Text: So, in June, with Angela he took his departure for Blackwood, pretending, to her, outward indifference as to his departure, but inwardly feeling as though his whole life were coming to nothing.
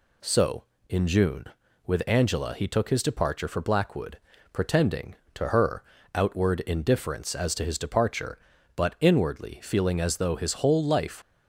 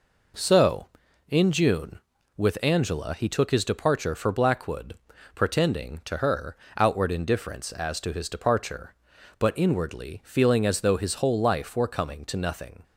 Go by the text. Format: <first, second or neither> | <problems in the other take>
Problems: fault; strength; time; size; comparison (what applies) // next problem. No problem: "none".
second | stops before "were coming to nothing"; at 11.2 s